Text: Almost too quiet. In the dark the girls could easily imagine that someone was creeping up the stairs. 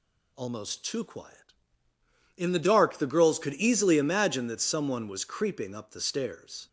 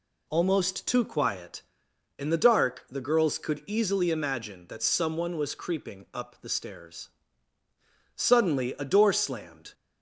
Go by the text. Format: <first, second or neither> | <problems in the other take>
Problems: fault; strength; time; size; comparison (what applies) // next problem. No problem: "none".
first | goes on to say "Suddenly a door slammed"; from 8.1 s on; 1.5 s long